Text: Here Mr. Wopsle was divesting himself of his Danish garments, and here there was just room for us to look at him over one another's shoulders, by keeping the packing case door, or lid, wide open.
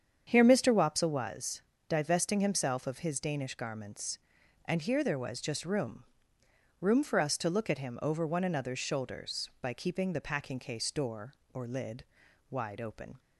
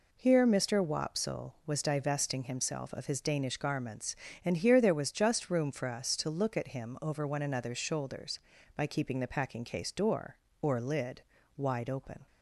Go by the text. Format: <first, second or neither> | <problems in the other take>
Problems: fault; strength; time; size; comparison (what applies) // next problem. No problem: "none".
second | starts louder than the rest; strong; until 1.2 s; 8 dB // pauses between "was" and "divesting"; slight; at 1.6 s; 0.26 s long // says "room" twice; at 6.8 s